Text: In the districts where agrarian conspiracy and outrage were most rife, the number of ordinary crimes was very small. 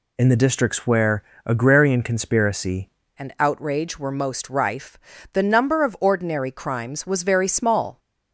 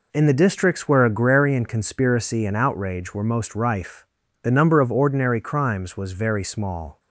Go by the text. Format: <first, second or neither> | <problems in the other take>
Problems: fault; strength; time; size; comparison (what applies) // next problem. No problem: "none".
second | pauses between "where" and "agrarian"; slight; at 1.2 s; 0.24 s long // changes voice at "and"; from 3.1 s on; 4.8 s long